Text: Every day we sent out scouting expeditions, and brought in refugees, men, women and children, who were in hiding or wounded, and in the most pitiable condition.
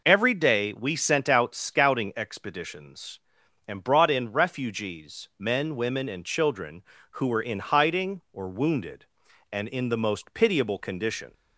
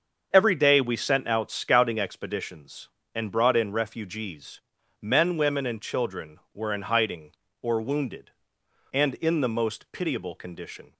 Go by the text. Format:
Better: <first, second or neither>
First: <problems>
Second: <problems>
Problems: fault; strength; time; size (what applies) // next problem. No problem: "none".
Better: first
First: none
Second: starts louder than the rest; until 1.3 s; 7 dB // skips "who"; at 6.4 s